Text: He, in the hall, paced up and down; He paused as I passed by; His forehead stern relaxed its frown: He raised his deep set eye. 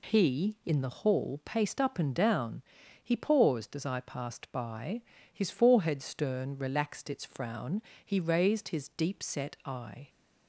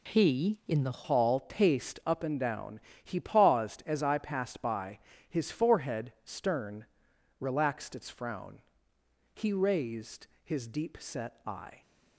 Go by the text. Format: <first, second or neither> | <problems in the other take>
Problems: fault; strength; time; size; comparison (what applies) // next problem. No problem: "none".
first | changes voice at "hall"; from 1.0 s on; 10.8 s long // pauses between "stern" and "relaxed"; noticeable; at 6.8 s; 0.56 s long